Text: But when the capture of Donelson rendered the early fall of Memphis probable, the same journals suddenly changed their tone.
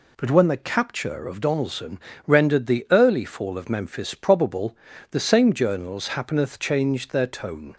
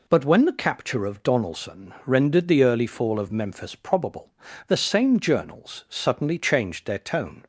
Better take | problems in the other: second | pauses between "Donelson" and "rendered"; slight; at 1.9 s; 0.26 s long // says "happeneth" for "suddenly"; at 6.0 s

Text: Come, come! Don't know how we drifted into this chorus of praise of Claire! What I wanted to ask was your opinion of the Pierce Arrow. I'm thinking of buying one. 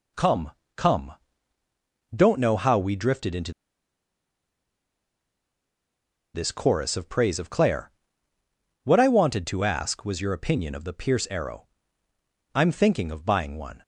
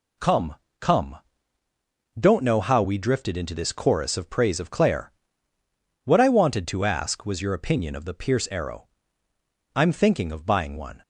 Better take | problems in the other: second | pauses between "into" and "this"; strong; at 3.5 s; 2.8 s long

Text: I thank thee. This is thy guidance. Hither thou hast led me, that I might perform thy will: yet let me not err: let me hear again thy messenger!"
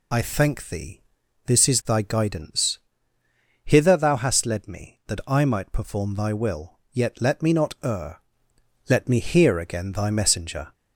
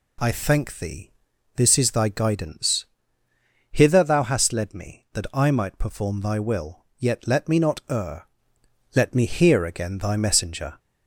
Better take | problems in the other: second | loses the start of "I"; at 0.1 s; 25 ms

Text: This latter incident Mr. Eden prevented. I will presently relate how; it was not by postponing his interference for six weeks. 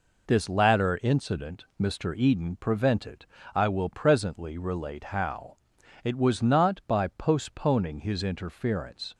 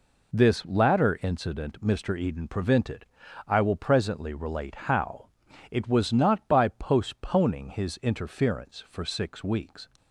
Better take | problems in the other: second | stops before "for six weeks"; at 9.1 s

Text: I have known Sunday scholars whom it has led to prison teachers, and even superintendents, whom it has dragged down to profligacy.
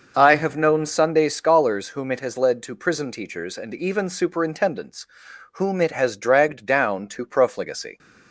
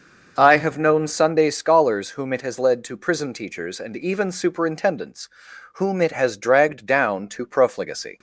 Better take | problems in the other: neither | starts louder than the rest; noticeable; the same in both

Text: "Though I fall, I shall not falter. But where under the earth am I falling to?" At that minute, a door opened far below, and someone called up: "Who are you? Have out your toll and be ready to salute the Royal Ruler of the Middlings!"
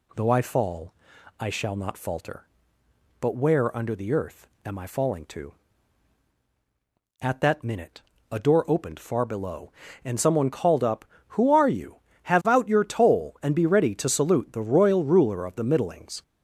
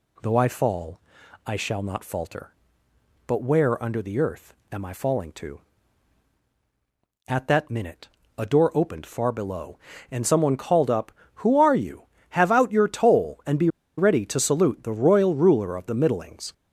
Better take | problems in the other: first | pauses between "earth" and "am"; slight; at 4.5 s; 0.18 s long; slight in the first // pauses between "be" and "ready"; slight; at 13.6 s; 0.29 s long

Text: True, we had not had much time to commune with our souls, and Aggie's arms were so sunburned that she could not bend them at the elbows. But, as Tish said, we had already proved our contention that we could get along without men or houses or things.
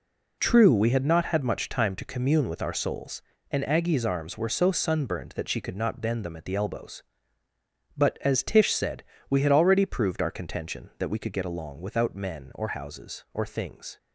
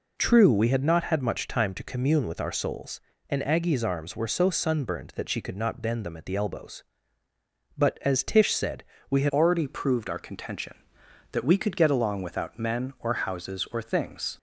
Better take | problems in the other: first | changes voice at "already"; from 9.3 s on; 5.0 s long

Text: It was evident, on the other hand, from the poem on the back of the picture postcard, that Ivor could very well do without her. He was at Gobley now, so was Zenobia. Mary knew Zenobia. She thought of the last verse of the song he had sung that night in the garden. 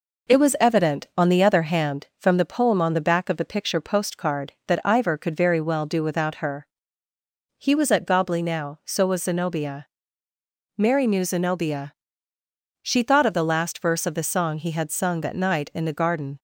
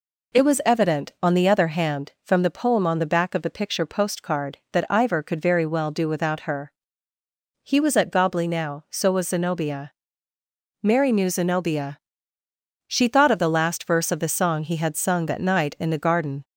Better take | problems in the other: second | gets quieter; slight; throughout; 2.5 dB

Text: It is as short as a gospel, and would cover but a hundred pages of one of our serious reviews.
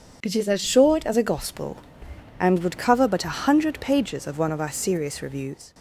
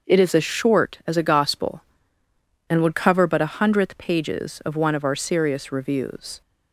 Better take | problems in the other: first | says "hundredth" for "hundred"; at 3.5 s

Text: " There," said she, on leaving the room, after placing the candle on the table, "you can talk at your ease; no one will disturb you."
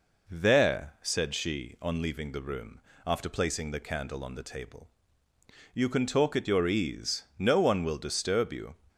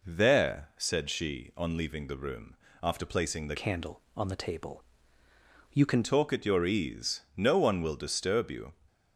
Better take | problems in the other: first | changes voice from "candle" to "can"; from 3.5 to 6.0 s; 2.5 s long

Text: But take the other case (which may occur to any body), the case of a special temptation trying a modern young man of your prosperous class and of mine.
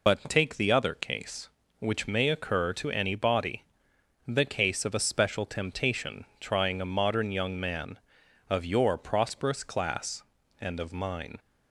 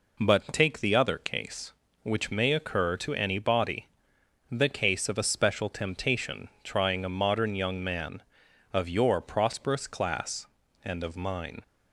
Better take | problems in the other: second | loses the start of "But"; at 0.0 s; 100 ms

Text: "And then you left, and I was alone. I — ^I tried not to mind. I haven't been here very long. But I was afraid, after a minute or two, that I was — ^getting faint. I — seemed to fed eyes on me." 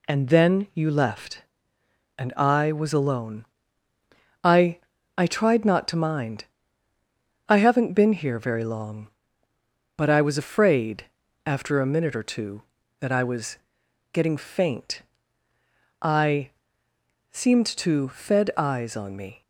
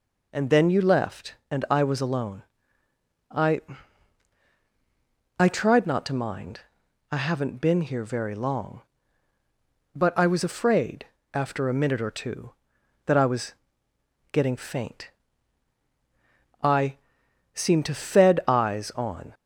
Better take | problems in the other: first | stops before "me"; at 19.3 s

